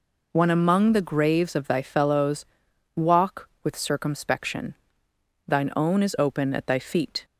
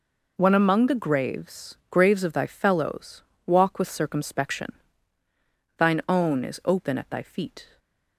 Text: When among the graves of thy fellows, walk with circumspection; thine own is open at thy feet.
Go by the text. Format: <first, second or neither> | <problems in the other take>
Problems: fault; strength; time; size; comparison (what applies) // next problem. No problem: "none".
first | says "graves" twice; at 1.8 s // stays silent after the last word; slight; from 7.6 s on; 0.5 s long